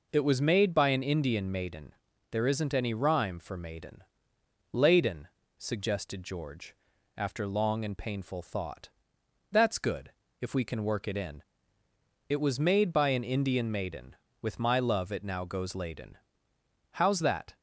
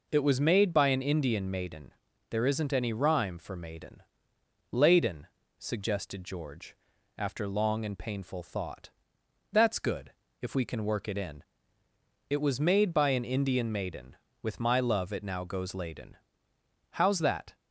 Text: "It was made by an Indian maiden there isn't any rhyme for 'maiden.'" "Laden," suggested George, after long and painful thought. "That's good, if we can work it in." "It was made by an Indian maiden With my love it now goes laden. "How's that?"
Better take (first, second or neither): neither